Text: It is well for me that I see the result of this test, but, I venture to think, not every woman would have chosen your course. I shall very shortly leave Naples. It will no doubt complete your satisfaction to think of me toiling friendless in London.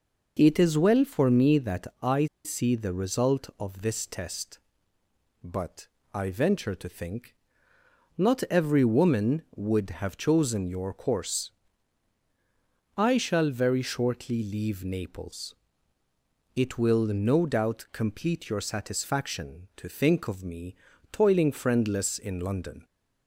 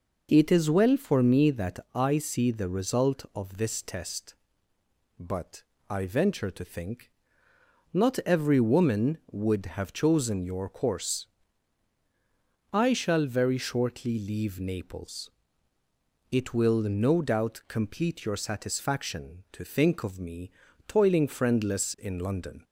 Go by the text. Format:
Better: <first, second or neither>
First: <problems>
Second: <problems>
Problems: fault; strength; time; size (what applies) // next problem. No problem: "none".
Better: second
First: pauses between "I" and "see"; slight; at 2.2 s; 0.19 s long // pauses between "me" and "toiling"; slight; at 20.7 s; 0.34 s long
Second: pauses between "me" and "toiling"; slight; at 20.5 s; 0.34 s long